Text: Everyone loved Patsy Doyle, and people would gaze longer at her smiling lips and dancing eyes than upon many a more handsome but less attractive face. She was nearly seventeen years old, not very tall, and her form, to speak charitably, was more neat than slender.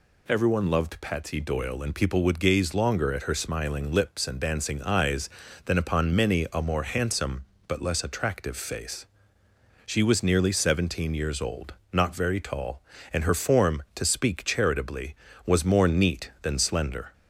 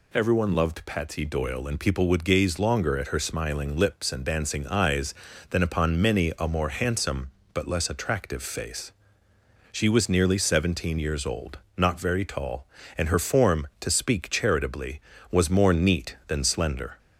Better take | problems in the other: neither | none

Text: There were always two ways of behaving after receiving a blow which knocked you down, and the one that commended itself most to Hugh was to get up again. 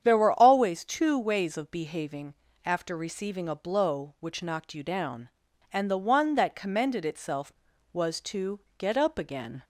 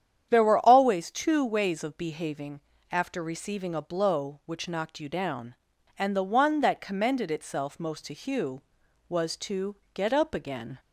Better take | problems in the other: second | starts louder than the rest; strong; until 1.0 s; 8.5 dB; strong in the second // pauses between "behaving" and "after"; slight; at 2.3 s; 0.30 s long; slight in the second // skips "most to Hugh"; at 7.7 s // pauses between "to" and "get"; slight; at 8.5 s; 0.18 s long; slight in the second

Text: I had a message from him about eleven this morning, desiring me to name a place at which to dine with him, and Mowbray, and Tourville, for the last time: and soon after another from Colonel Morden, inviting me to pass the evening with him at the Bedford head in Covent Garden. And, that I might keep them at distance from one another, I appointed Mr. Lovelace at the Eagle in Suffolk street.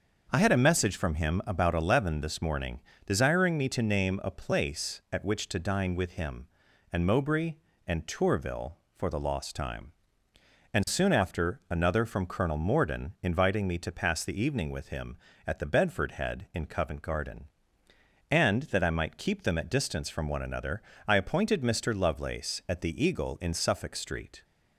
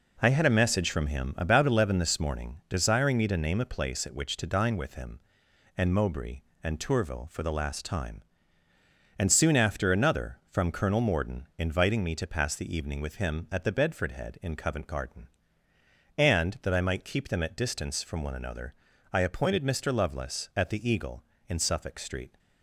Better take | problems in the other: second | starts louder than the rest; until 1.3 s; 6.5 dB // says "lost" for "last"; at 9.1 s

